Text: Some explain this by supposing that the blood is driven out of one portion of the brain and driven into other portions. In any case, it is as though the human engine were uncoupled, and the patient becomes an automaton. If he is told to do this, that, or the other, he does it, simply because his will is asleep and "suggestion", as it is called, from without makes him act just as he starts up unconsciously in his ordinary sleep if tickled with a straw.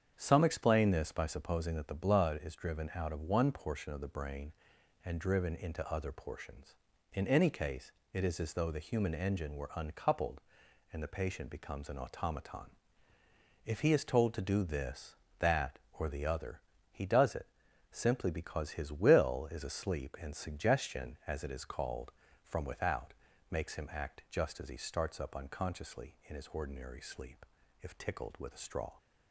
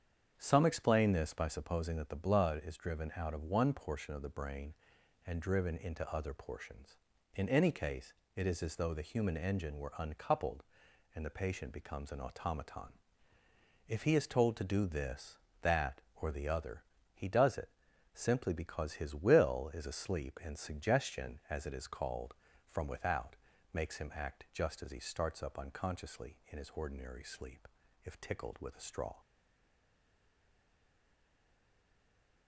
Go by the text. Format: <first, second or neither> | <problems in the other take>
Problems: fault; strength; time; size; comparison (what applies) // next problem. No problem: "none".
first | starts louder than the rest; strong; until 1.3 s; 8 dB; strong in the first // pauses between "without" and "makes"; slight; at 23.3 s; 0.34 s long; slight in the first // pauses between "sleep" and "if"; slight; at 27.6 s; 0.36 s long; slight in the first // stays silent after the last word; strong; from 29.1 s on; 3.3 s long